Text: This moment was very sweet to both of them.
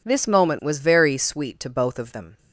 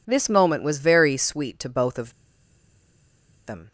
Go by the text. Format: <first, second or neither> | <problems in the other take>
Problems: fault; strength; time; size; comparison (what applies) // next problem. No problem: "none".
first | pauses between "of" and "them"; strong; at 2.1 s; 1.3 s long